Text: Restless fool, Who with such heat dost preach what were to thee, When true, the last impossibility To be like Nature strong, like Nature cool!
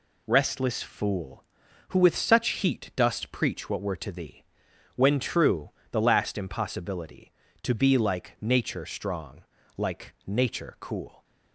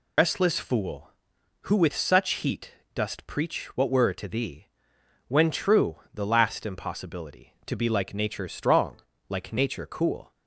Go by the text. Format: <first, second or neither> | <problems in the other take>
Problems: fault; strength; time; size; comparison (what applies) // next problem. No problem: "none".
first | loses the start of "Restless"; at 0.1 s; 95 ms // pauses between "heat" and "dost"; slight; at 2.7 s; 0.20 s long